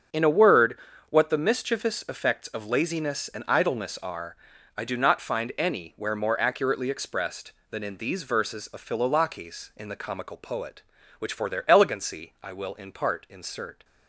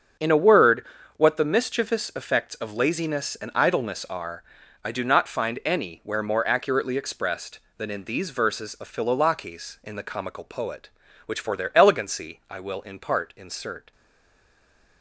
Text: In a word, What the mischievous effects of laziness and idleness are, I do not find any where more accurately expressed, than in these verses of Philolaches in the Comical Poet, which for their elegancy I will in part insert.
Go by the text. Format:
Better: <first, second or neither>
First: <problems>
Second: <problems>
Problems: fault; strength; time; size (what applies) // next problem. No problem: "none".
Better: first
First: starts louder than the rest; until 1.4 s; 6.5 dB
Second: starts louder than the rest; until 1.5 s; 6.5 dB // stays silent after the last word; from 13.9 s on; 1.1 s long